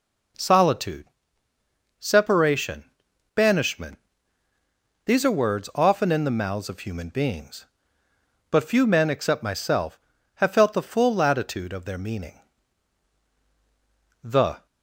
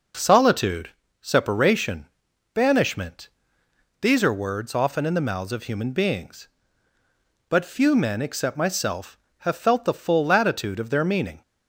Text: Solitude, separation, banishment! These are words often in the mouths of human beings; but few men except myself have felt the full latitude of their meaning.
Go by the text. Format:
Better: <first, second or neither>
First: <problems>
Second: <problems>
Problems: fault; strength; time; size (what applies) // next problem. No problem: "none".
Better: second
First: goes on to say "The"; slight; from 14.2 s on; 0.44 s long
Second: none